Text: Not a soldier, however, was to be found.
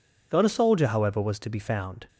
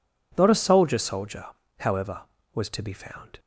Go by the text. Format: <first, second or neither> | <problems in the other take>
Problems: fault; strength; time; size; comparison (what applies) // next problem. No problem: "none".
first | says "soldier" twice; at 0.9 s